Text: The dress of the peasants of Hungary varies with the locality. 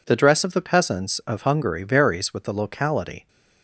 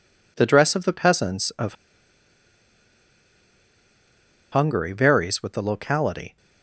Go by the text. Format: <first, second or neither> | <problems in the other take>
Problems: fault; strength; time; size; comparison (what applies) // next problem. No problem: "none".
first | pauses between "of" and "Hungary"; strong; at 1.7 s; 2.7 s long